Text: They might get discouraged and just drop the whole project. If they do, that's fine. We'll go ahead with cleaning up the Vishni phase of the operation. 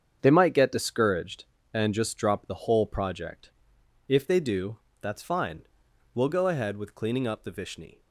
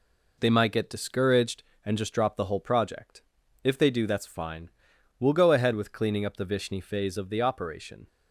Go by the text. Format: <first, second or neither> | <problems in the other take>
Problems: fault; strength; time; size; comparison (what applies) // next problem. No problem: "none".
second | starts louder than the rest; strong; until 1.2 s; 7.5 dB // stops before "phase of the operation"; at 7.9 s